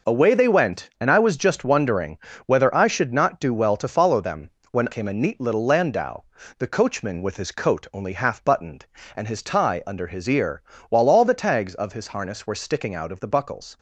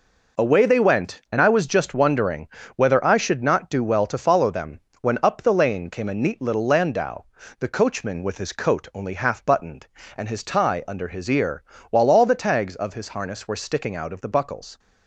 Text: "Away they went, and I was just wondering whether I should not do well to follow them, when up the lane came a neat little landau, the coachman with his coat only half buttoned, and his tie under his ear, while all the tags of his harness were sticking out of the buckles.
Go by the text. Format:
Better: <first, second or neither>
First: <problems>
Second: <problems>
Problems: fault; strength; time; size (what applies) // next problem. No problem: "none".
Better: second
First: pauses between "wondering" and "whether"; slight; at 2.1 s; 0.30 s long // skips "up the lane"; at 4.8 s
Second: pauses between "wondering" and "whether"; slight; at 2.4 s; 0.30 s long